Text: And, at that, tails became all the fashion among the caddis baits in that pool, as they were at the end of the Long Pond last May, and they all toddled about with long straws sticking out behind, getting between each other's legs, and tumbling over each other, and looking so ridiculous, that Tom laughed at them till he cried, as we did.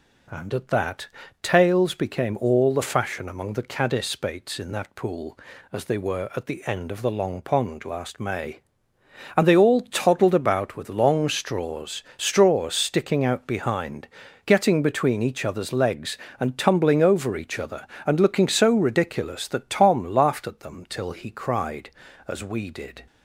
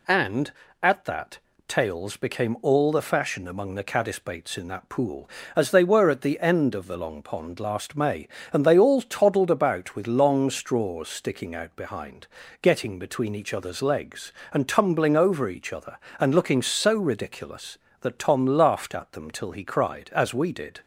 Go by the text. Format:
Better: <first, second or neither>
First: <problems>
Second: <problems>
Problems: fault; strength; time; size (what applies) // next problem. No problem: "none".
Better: second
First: says "straws" twice; at 12.1 s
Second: none